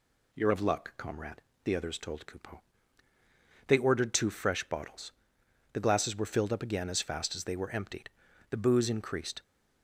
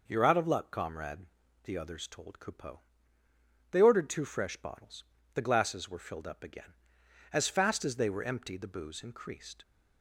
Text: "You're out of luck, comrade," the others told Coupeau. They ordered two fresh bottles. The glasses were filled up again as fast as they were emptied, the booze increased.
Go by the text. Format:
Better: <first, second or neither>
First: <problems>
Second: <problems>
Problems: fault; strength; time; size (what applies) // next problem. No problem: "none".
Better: second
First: skips "out"; at 0.5 s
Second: none